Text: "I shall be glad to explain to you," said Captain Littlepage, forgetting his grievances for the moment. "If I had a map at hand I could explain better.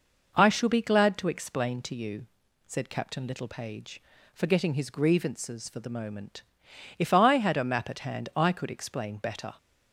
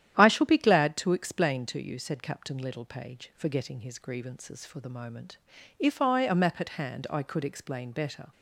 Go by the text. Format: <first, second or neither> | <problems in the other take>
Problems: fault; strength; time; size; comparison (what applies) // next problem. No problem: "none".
first | starts louder than the rest; strong; until 1.2 s; 11 dB // skips "had"; at 6.2 s